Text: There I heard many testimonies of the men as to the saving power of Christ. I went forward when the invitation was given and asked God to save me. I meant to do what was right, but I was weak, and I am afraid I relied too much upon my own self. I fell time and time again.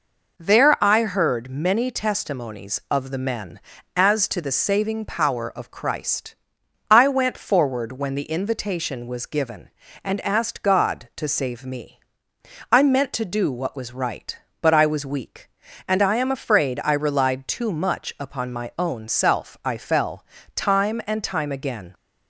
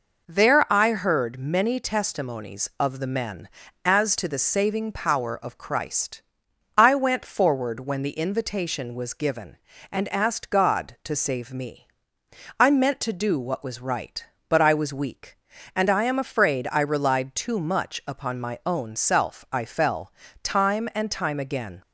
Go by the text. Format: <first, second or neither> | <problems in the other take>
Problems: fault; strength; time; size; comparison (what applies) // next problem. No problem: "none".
neither | pauses between "fell" and "time"; slight; the same in both